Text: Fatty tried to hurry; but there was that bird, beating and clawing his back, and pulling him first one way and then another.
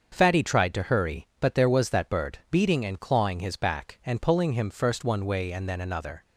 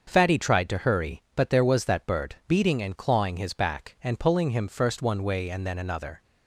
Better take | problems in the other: neither | starts louder than the rest; the same in both

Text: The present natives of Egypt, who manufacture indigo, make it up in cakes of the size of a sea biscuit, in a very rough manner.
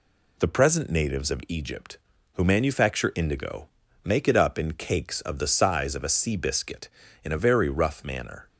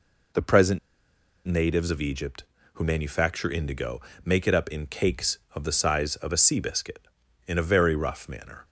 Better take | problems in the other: first | pauses between "present" and "natives"; noticeable; at 0.7 s; 0.67 s long

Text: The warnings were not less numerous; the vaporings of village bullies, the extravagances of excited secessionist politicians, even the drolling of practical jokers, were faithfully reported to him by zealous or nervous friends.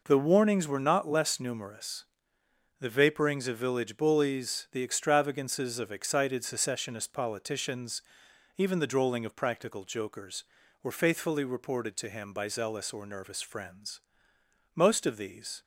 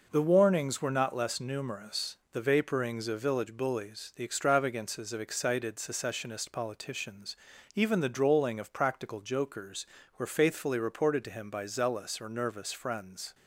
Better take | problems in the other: second | goes on to say "Most of these"; noticeable; from 14.7 s on; 0.88 s long

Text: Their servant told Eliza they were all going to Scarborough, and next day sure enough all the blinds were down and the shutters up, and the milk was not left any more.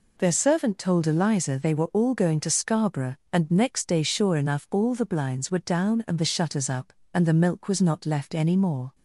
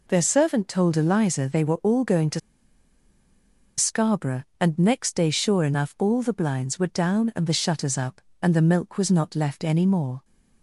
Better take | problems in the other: first | pauses between "to" and "Scarborough"; strong; at 2.3 s; 1.3 s long

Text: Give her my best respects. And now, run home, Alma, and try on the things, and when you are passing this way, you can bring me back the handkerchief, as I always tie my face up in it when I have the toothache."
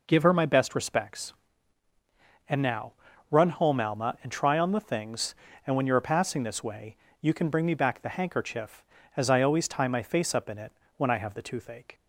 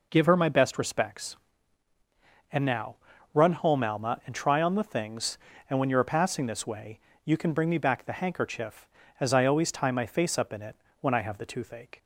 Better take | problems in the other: neither | pauses between "it" and "when"; slight; the same in both

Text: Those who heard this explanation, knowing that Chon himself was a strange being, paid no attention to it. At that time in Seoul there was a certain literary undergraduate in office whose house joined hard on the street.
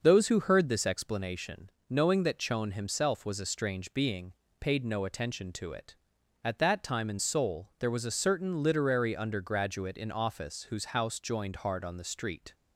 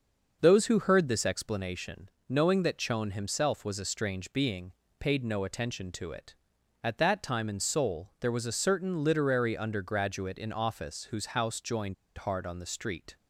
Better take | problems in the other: first | starts louder than the rest; noticeable; until 1.4 s; 6 dB // pauses between "joined" and "hard"; slight; at 11.9 s; 0.23 s long

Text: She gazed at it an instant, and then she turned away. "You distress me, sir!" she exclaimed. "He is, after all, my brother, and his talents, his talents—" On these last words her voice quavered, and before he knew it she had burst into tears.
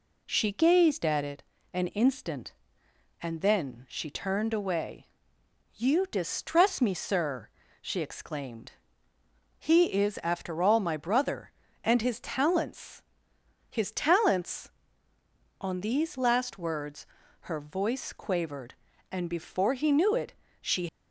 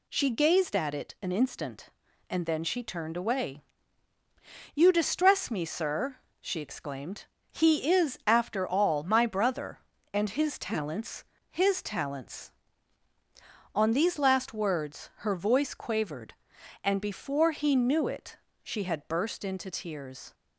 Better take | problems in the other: second | pauses between "it" and "an"; slight; at 1.4 s; 0.30 s long // pauses between "words" and "her"; slight; at 17.0 s; 0.36 s long // pauses between "it" and "she"; slight; at 20.3 s; 0.30 s long; slight in the second // stops before "had burst into tears"; at 20.8 s

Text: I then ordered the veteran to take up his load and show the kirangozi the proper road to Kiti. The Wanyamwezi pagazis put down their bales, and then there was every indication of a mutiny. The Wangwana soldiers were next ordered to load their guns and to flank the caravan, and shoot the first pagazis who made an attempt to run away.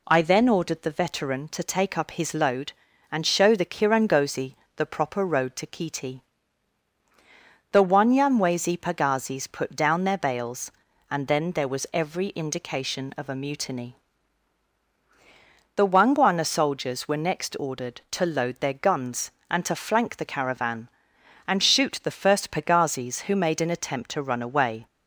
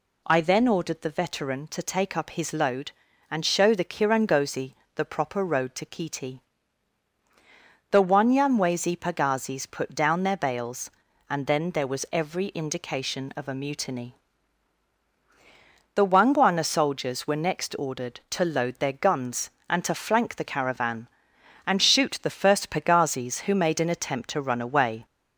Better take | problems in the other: first | gets louder; slight; throughout; 2.5 dB // pauses between "kirangozi" and "the"; slight; at 4.7 s; 0.20 s long; slight in the first

